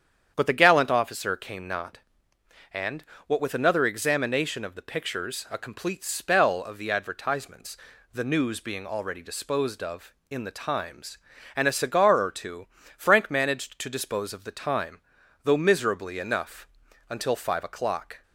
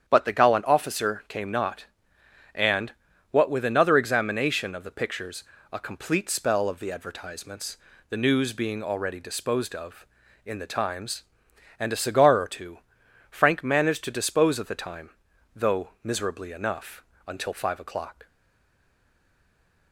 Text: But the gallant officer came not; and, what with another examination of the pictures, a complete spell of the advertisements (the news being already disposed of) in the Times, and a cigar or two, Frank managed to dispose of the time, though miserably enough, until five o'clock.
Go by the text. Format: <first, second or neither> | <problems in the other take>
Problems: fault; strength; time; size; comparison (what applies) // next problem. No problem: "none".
first | starts louder than the rest; strong; until 1.1 s; 9 dB; strong in the first // pauses between "though" and "miserably"; slight; at 15.8 s; 0.16 s long // stays silent after the last word; noticeable; from 18.2 s on; 1.7 s long